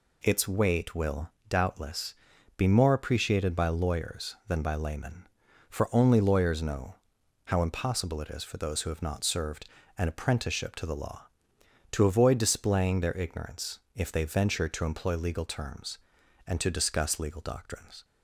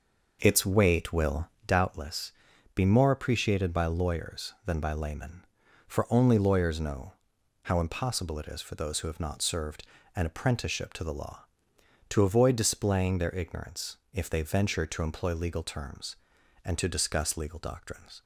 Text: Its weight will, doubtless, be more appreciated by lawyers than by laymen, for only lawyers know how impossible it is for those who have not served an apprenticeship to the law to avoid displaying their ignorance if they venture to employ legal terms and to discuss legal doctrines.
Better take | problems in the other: first | starts louder than the rest; noticeable; until 2.0 s; 6 dB // pauses between "know" and "how"; noticeable; at 7.1 s; 0.52 s long; noticeable in the first // pauses between "served" and "an"; slight; at 9.8 s; 0.30 s long; slight in the first // pauses between "ignorance" and "if"; slight; at 13.9 s; 0.16 s long; slight in the first

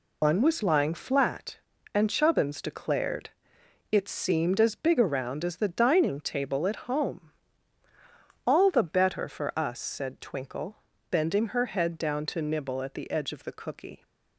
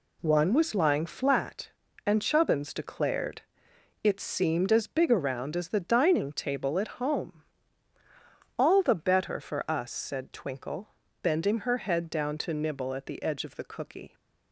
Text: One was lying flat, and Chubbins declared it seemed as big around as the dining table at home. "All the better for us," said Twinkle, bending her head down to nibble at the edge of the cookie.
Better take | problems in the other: second | loses the start of "One"; at 0.2 s; 150 ms // pauses between "declared" and "it"; noticeable; at 3.2 s; 0.64 s long; noticeable in the second

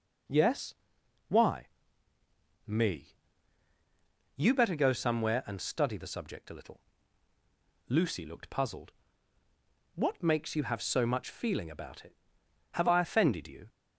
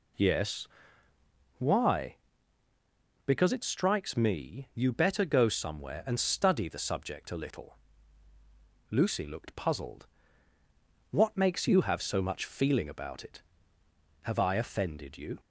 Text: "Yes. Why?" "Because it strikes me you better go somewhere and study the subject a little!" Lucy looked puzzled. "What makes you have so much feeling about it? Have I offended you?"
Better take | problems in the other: second | skips "Because it strikes"; at 2.1 s // pauses between "me" and "you"; at 3.1 s; 1.2 s long

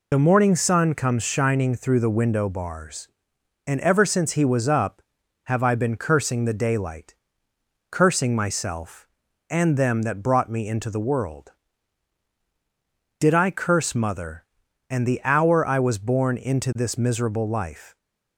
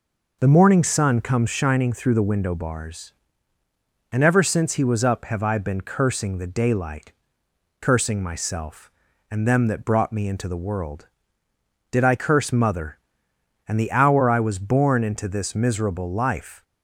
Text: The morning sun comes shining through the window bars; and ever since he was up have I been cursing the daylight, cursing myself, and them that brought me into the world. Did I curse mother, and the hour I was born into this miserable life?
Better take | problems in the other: second | loses the start of "The"; at 0.1 s; 55 ms

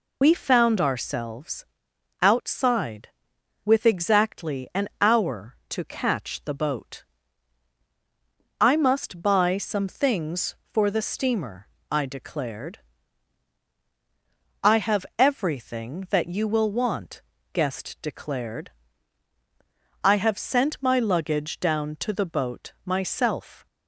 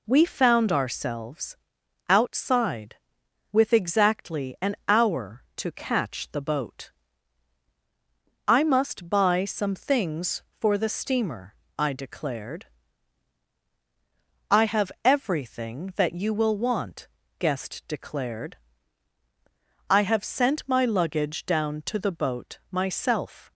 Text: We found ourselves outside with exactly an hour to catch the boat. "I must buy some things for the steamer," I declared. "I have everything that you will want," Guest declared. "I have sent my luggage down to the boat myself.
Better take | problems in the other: second | loses the start of "We"; at 0.2 s; 55 ms // pauses between "ourselves" and "outside"; noticeable; at 1.6 s; 0.56 s long; noticeable in the second

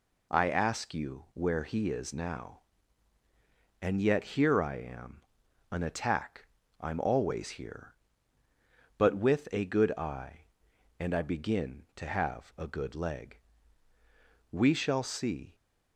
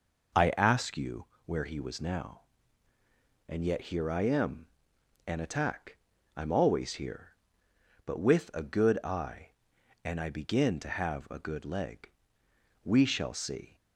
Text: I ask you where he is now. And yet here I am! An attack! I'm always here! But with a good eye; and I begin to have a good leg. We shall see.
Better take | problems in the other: first | pauses between "you" and "where"; slight; at 1.2 s; 0.18 s long // says "was" for "is"; at 1.7 s

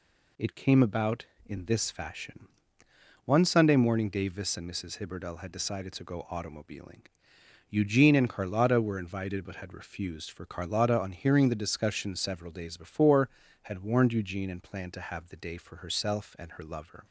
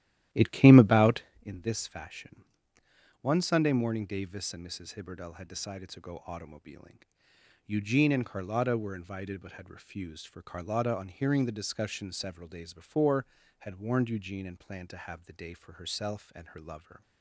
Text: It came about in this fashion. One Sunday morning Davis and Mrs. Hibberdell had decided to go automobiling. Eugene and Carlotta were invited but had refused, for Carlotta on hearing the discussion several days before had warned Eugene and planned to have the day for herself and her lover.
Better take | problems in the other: first | starts louder than the rest; strong; until 1.5 s; 13 dB

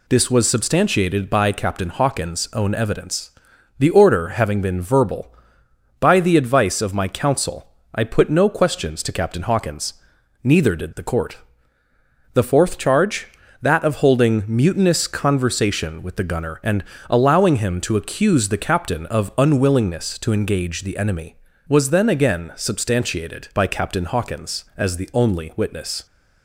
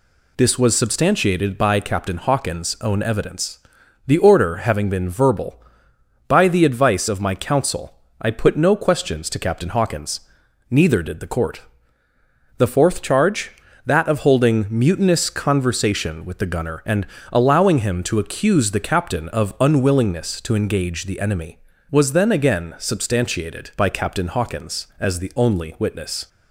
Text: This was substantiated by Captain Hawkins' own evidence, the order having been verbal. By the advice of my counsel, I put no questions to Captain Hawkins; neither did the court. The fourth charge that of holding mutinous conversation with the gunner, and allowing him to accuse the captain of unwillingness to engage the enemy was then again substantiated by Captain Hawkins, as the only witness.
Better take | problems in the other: neither | pauses between "and" and "allowing"; slight; the same in both

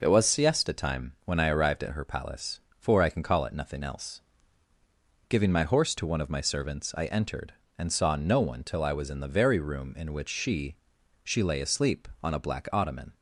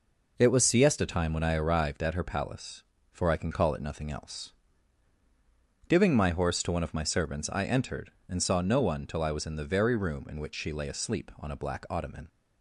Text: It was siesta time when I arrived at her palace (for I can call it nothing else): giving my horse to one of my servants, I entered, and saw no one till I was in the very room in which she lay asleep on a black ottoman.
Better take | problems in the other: second | says "she" twice; at 11.2 s

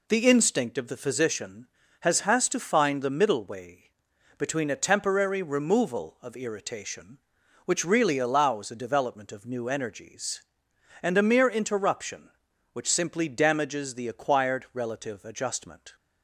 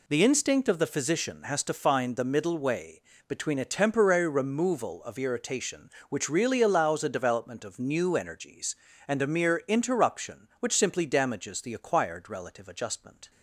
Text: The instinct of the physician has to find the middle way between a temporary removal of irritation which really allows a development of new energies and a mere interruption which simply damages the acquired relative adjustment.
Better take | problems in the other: second | says "has" twice; at 2.2 s // pauses between "way" and "between"; noticeable; at 3.8 s; 0.48 s long; slight in the second

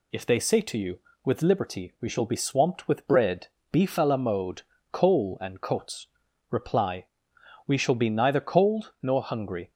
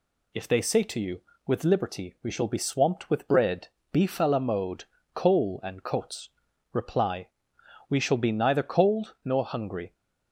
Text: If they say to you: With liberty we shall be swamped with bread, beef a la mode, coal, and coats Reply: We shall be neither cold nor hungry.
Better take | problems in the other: neither | pauses between "coats" and "Reply"; the same in both

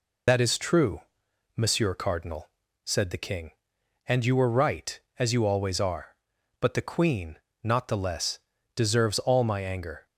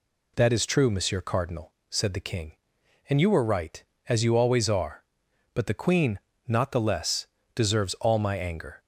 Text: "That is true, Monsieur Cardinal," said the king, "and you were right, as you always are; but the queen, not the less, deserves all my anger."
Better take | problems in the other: second | loses the start of "That"; at 0.2 s; 80 ms

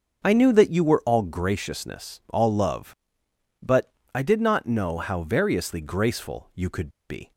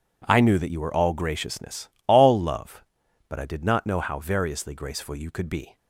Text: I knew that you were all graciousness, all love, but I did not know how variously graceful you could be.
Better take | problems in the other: second | starts louder than the rest; until 1.2 s; 6.5 dB // pauses between "but" and "I"; slight; at 3.9 s; 0.22 s long // pauses between "could" and "be"; slight; at 6.8 s; 0.18 s long

